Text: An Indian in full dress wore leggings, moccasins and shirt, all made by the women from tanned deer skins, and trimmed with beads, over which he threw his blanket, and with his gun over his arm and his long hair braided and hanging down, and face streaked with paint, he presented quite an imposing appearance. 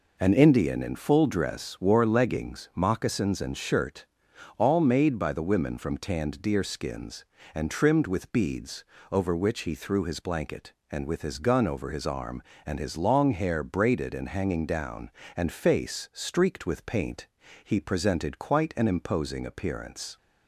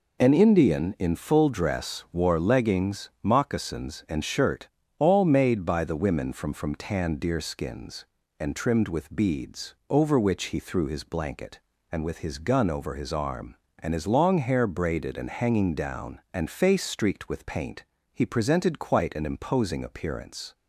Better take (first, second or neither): first